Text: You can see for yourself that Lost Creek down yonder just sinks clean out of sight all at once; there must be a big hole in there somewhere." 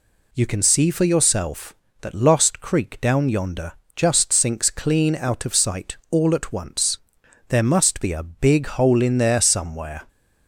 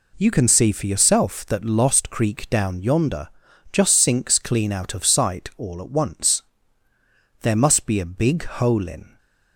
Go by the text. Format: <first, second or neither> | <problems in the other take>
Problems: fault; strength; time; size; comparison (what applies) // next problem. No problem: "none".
first | pauses between "yonder" and "just"; at 3.2 s; 0.42 s long; slight in the first // stops before "there somewhere"; at 9.1 s